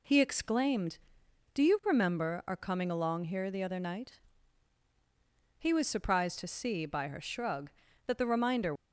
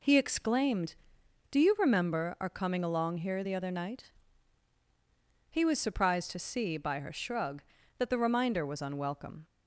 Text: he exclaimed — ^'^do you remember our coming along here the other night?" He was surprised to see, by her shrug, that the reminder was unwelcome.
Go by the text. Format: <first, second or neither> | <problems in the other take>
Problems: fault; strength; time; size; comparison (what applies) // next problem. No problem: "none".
second | stops before "was unwelcome"; at 8.7 s